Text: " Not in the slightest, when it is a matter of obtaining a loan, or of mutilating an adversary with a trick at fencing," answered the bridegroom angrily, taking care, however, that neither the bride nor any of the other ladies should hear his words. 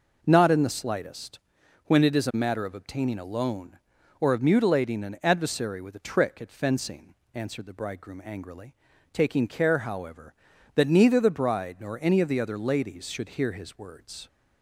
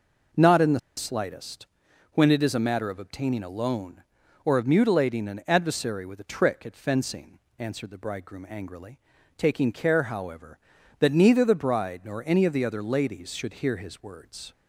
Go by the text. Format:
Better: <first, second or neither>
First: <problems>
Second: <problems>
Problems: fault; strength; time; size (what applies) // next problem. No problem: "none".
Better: first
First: none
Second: pauses between "the" and "slightest"; slight; at 0.7 s; 0.18 s long